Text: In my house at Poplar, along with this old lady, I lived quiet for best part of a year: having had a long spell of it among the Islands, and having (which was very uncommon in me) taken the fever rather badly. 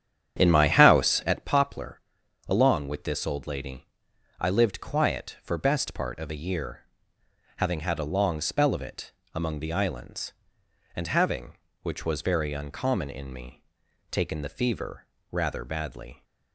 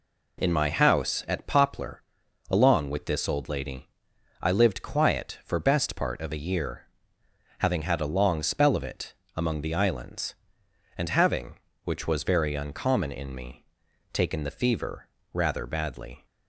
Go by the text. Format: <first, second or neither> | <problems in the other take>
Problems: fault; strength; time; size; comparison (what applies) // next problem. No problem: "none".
second | starts louder than the rest; strong; until 1.5 s; 9.5 dB // pauses between "it" and "among"; slight; at 9.1 s; 0.22 s long; slight in the second // pauses between "fever" and "rather"; slight; at 15.0 s; 0.24 s long; slight in the second